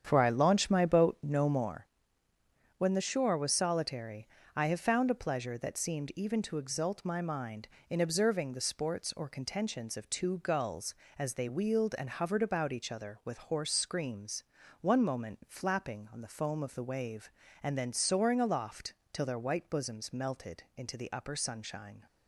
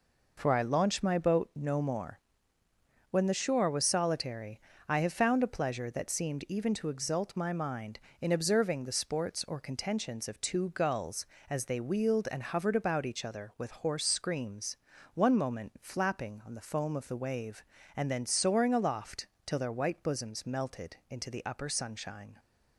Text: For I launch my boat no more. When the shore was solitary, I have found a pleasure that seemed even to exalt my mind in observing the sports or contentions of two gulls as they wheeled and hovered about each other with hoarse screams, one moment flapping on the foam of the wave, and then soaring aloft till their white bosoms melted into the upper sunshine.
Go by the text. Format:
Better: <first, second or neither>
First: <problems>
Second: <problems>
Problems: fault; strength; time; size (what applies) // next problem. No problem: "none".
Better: second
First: starts louder than the rest; strong; until 1.8 s; 8.5 dB // pauses between "aloft" and "till"; slight; at 18.9 s; 0.22 s long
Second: pauses between "aloft" and "till"; slight; at 19.2 s; 0.22 s long